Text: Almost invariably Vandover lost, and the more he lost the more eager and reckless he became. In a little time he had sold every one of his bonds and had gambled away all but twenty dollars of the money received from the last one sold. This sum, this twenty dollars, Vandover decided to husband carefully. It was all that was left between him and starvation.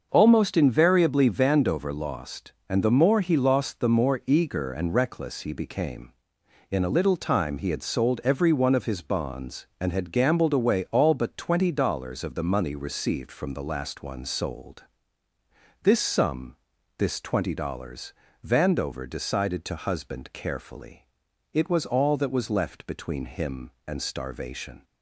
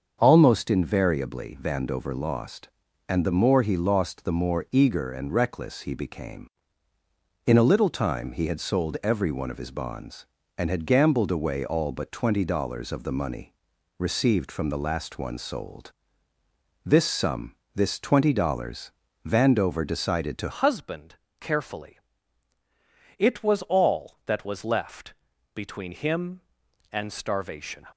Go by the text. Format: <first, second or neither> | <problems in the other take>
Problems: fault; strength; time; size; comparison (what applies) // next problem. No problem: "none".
first | starts louder than the rest; until 1.2 s; 7 dB; also in the first // pauses between "money" and "received"; at 13.5 s; 0.44 s long // changes voice at "husband"; from 20.5 s on; 7.3 s long // pauses between "husband" and "carefully"; slight; at 21.1 s; 0.26 s long // pauses between "left" and "between"; at 25.1 s; 0.40 s long